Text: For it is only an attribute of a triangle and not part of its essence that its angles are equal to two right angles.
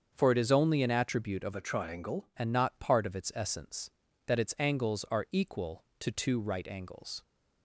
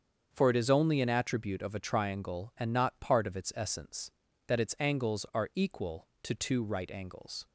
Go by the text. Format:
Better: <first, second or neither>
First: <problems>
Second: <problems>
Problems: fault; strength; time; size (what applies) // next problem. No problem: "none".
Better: second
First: starts louder than the rest; until 1.1 s; 7 dB // changes voice from "a" to "triangle"; from 1.5 to 2.2 s; 0.7 s long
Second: starts louder than the rest; until 1.3 s; 7 dB